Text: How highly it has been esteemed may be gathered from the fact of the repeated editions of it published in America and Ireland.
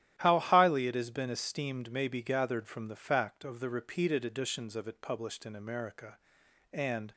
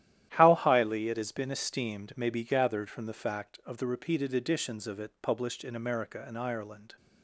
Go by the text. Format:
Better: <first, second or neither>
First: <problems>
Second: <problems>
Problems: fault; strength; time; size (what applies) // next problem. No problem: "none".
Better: second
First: starts louder than the rest; strong; until 1.1 s; 12.5 dB // stops before "Ireland"; at 7.1 s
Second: starts louder than the rest; strong; until 1.3 s; 12.5 dB